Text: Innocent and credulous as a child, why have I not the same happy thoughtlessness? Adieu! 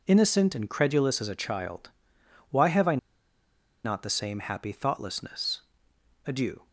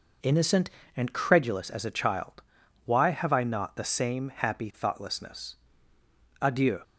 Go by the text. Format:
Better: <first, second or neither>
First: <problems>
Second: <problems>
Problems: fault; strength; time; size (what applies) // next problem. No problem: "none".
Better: second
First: pauses between "I" and "not"; noticeable; at 2.9 s; 0.88 s long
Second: none